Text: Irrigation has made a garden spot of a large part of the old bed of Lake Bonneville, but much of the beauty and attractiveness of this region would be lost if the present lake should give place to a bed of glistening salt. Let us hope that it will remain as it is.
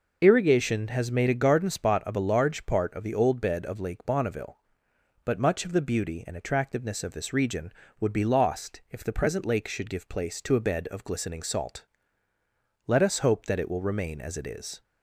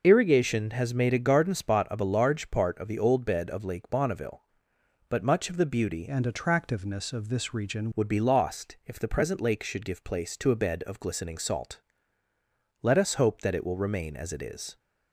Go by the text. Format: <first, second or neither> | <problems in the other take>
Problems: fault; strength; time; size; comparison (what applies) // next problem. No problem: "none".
first | changes voice from "and" to "region"; from 6.0 to 7.8 s; 1.8 s long